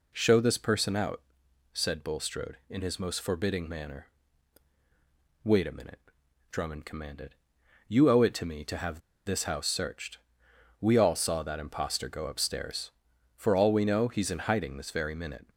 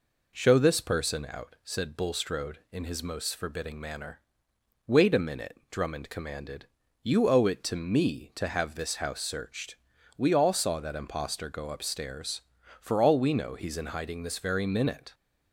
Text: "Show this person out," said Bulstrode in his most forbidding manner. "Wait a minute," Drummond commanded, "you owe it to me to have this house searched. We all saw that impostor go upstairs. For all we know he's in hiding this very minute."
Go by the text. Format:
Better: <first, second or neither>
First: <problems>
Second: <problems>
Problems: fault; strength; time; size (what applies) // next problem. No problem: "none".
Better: second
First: pauses between "have" and "this"; slight; at 8.9 s; 0.26 s long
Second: none